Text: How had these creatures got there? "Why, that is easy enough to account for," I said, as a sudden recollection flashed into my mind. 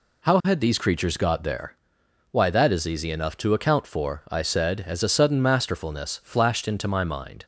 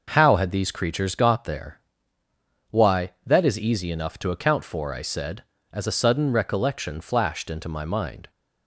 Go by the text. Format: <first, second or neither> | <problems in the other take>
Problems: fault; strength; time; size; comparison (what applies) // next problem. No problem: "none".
second | says "masterfulness" for "recollection"; at 5.4 s